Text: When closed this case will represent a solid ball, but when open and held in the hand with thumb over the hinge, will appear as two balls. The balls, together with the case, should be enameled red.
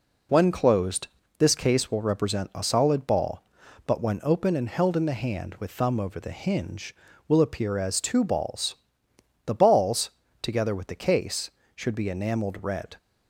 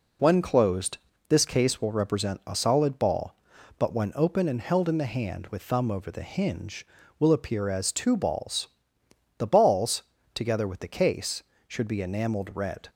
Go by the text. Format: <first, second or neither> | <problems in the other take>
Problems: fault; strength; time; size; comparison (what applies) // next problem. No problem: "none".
neither | pauses between "closed" and "this"; slight; the same in both